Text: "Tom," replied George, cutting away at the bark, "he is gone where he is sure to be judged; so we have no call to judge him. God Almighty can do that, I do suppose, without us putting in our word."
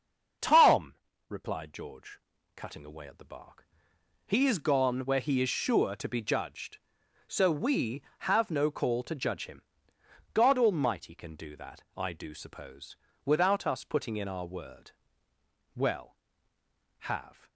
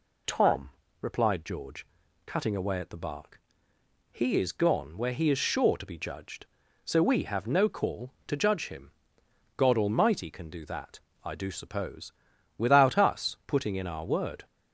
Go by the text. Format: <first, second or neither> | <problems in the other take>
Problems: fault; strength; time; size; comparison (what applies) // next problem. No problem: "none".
second | starts louder than the rest; until 1.7 s; 6.5 dB // goes on to say "Well have"; strong; from 15.7 s on; 1.7 s long